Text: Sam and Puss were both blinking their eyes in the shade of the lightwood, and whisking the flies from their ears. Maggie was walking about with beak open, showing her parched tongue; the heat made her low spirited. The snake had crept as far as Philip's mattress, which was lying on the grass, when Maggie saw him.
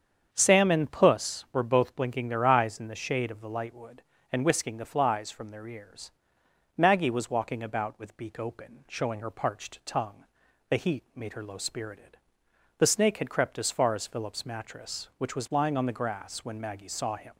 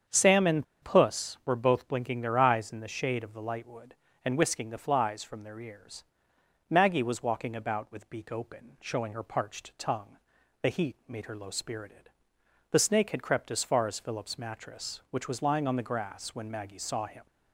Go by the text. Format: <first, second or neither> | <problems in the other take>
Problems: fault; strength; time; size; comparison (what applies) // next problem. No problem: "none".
first | starts louder than the rest; strong; until 1.2 s; 7.5 dB; strong in the first // pauses between "and" and "Puss"; slight; at 0.6 s; 0.17 s long